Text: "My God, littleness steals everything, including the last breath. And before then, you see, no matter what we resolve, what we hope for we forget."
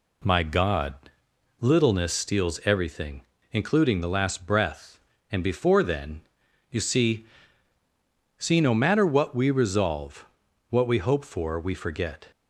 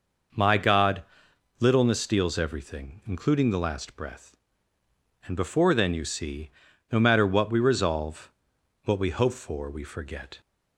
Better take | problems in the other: second | says "see" twice; at 8.3 s

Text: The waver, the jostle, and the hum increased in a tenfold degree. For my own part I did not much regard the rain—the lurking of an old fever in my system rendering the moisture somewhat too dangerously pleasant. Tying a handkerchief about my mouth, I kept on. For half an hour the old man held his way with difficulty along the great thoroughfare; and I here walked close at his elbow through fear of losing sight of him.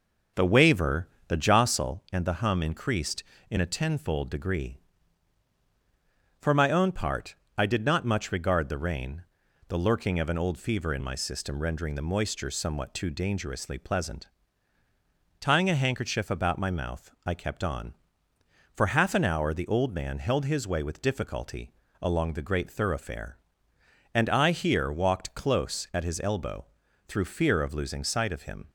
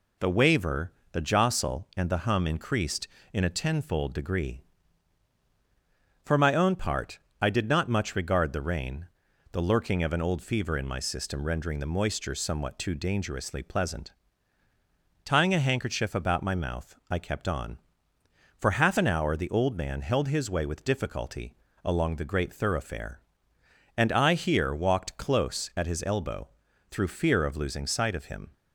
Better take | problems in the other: second | starts louder than the rest; until 1.9 s; 6.5 dB // pauses between "part" and "I"; slight; at 7.3 s; 0.22 s long; slight in the second // pauses between "difficulty" and "along"; slight; at 21.7 s; 0.28 s long; slight in the second // pauses between "elbow" and "through"; at 26.6 s; 0.42 s long; also in the second

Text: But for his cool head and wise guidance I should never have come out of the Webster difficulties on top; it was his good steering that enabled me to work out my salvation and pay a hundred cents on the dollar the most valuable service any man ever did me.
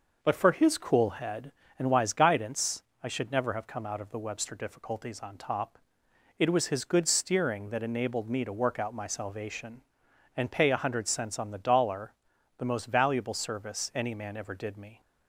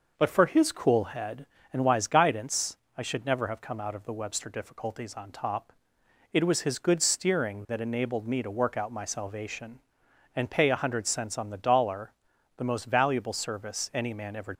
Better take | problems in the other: first | pauses between "guidance" and "I"; slight; at 2.7 s; 0.20 s long; slight in the first // pauses between "dollar" and "the"; noticeable; at 12.1 s; 0.46 s long; noticeable in the first // stops before "did me"; at 14.5 s

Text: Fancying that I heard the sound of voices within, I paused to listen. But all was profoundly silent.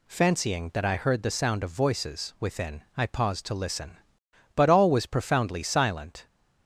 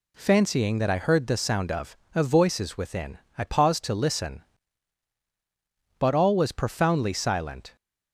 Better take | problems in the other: first | says "of" twice; at 2.1 s

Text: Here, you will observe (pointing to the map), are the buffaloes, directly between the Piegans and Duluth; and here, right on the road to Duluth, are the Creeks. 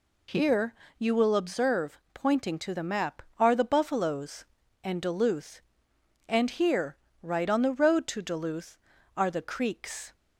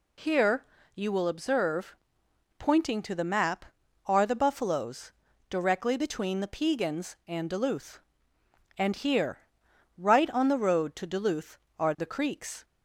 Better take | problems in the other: second | skips "directly between the Piegans"; at 4.6 s

